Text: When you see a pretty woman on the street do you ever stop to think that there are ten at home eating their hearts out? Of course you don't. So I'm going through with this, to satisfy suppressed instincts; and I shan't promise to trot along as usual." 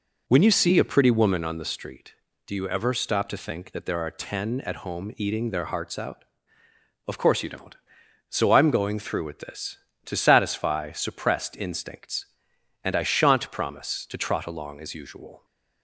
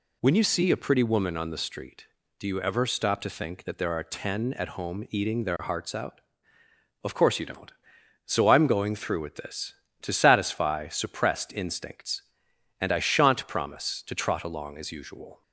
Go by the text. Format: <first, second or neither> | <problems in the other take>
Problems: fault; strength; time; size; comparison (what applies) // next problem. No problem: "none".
second | starts louder than the rest; until 1.5 s; 4 dB